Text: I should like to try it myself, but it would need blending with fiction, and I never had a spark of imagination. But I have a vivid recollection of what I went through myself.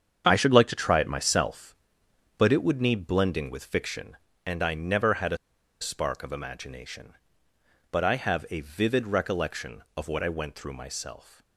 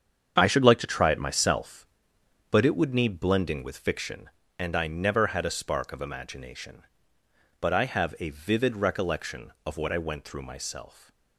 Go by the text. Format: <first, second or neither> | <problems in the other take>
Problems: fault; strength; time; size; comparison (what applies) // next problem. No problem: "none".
second | starts louder than the rest; strong; until 1.3 s; 7.5 dB; strong in the second // pauses between "a" and "spark"; at 5.3 s; 0.44 s long